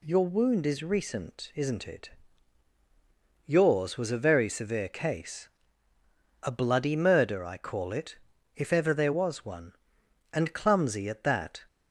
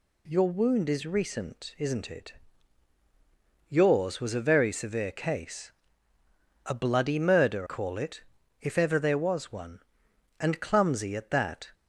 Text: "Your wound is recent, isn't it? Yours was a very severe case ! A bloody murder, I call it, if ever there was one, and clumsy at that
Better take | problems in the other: first | skips "I"; at 7.6 s

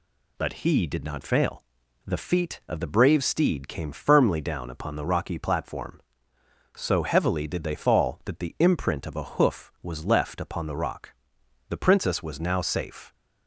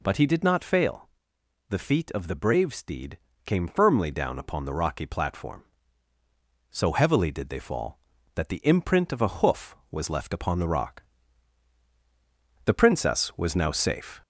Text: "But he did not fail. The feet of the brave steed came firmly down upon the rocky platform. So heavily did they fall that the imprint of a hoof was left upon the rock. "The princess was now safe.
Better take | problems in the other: first | gets louder; slight; throughout; 2 dB // pauses between "steed" and "came"; slight; at 3.1 s; 0.28 s long

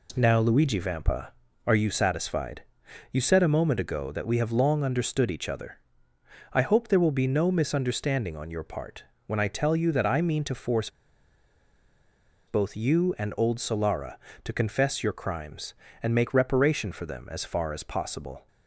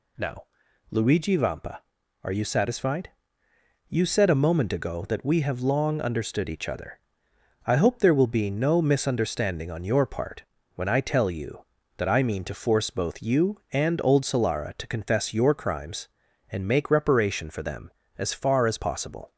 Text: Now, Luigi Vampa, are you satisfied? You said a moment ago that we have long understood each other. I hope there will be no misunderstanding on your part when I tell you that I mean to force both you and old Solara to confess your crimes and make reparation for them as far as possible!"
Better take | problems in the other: second | pauses between "part" and "when"; slight; at 9.0 s; 0.22 s long; slight in the second // pauses between "force" and "both"; strong; at 10.8 s; 1.5 s long

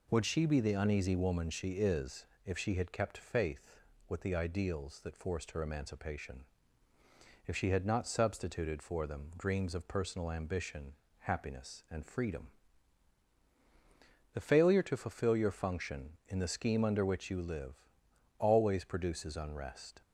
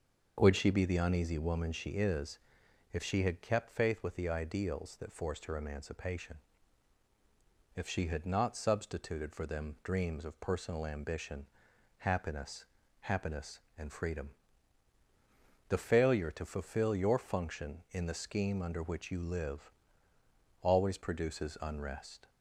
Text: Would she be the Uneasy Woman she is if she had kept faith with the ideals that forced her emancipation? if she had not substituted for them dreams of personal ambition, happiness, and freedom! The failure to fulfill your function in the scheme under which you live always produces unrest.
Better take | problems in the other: first | starts louder than the rest; until 1.3 s; 6 dB // pauses between "is" and "if"; noticeable; at 2.3 s; 0.54 s long; slight in the first // says "happiness" twice; at 13.0 s // pauses between "live" and "always"; noticeable; at 19.7 s; 0.90 s long; noticeable in the first

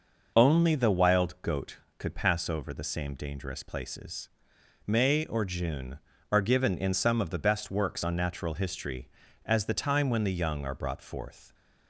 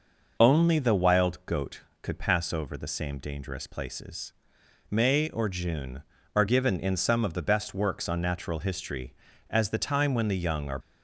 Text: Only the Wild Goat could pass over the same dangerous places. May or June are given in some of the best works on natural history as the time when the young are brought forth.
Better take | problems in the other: first | stops before "brought forth"; at 10.8 s

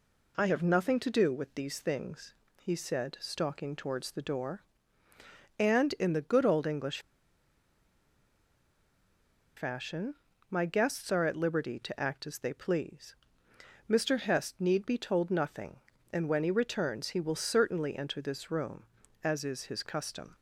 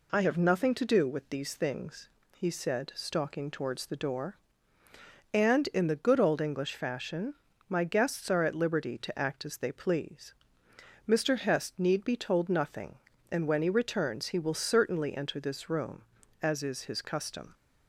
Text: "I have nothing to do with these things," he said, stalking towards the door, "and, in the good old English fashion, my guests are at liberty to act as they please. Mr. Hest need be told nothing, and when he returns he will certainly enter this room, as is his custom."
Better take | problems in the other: second | pauses between "English" and "fashion"; strong; at 6.9 s; 2.5 s long

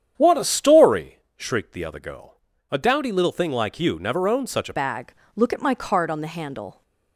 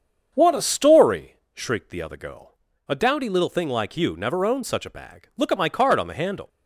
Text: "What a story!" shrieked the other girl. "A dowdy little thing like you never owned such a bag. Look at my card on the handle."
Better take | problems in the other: second | starts louder than the rest; strong; until 1.1 s; 9 dB; strong in the second // changes voice at "bag"; from 4.7 s on; 2.1 s long

